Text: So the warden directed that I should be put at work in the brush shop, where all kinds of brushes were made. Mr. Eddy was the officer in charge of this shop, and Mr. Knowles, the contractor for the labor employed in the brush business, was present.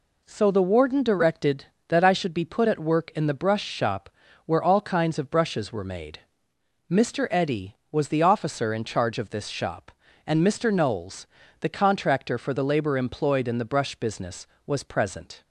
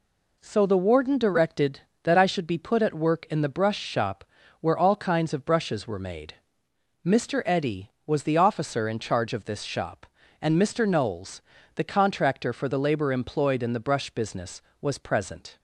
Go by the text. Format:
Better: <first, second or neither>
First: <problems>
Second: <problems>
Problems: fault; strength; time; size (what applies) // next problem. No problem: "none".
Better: neither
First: none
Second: none